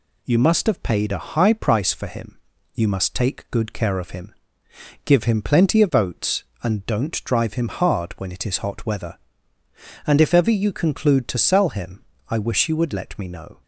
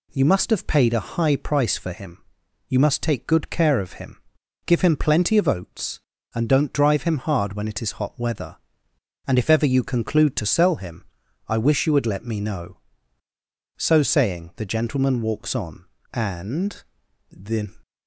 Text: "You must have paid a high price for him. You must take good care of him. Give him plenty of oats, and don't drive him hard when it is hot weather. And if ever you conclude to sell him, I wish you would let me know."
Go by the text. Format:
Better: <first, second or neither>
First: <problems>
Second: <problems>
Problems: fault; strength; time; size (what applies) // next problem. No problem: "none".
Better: first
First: none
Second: goes on to say "So saying the gentleman walks on and the"; strong; from 13.7 s on; 3.9 s long